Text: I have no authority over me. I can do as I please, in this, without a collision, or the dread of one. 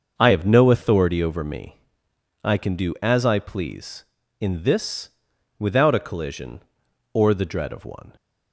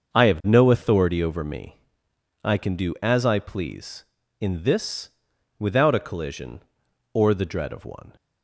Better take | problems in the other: neither | starts louder than the rest; the same in both

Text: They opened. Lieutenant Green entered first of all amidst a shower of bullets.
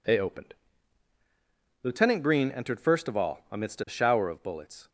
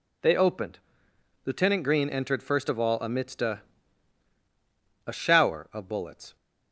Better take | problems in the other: first | says "a" twice; at 5.0 s

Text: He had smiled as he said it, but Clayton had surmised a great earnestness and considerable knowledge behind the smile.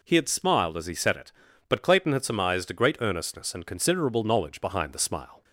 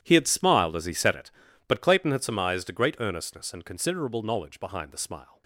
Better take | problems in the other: first | gets quieter; strong; throughout; 16 dB

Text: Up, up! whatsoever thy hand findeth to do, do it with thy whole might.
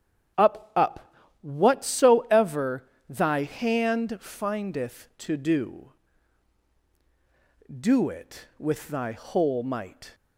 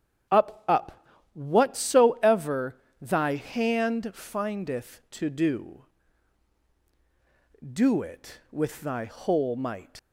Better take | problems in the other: first | starts louder than the rest; strong; until 1.6 s; 8.5 dB; strong in the first // pauses between "whatsoever" and "thy"; slight; at 2.8 s; 0.20 s long; slight in the first // leaves "might" unfinished; at 9.9 s; 80 ms

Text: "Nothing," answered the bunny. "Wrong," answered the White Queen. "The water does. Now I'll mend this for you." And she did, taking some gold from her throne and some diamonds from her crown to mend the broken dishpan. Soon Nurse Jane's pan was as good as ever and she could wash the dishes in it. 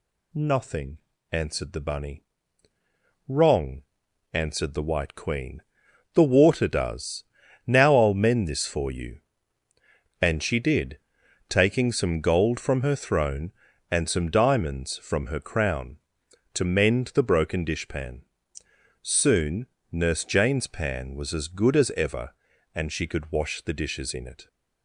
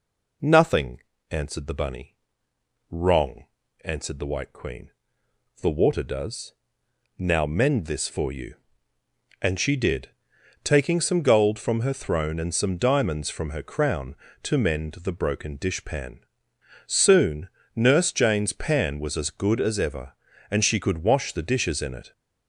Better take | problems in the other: first | skips "I'll"; at 7.4 s // pauses between "Soon" and "Nurse"; slight; at 17.4 s; 0.28 s long; slight in the first

